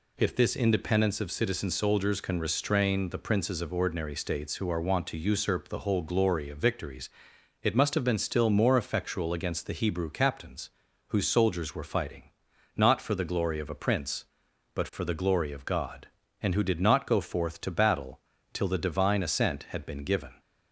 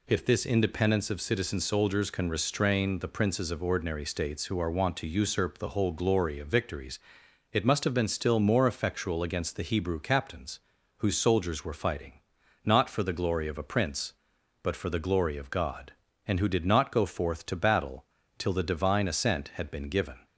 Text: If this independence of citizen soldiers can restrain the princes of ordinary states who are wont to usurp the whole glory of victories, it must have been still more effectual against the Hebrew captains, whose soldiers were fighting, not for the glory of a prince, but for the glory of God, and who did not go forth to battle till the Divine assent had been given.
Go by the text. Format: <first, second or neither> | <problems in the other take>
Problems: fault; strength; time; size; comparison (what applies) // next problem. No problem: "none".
neither | pauses between "battle" and "till"; slight; the same in both